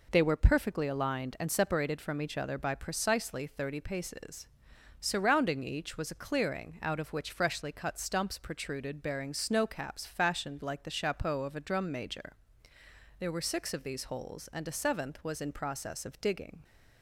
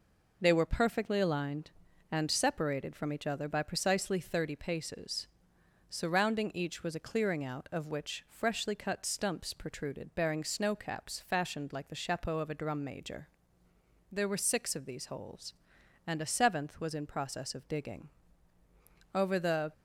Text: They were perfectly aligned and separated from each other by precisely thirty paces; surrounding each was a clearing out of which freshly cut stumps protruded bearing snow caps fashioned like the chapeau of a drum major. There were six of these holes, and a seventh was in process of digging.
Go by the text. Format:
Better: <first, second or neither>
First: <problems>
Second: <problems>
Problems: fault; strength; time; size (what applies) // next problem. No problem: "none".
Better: first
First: none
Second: goes on to say "Over the"; from 19.1 s on; 0.58 s long